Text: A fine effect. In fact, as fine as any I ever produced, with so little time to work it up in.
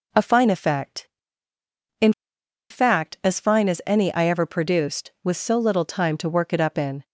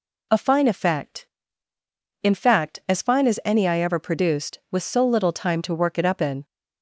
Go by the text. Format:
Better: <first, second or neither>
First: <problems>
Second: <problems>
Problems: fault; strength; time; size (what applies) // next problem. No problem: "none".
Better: second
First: pauses between "In" and "fact"; noticeable; at 2.1 s; 0.57 s long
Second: none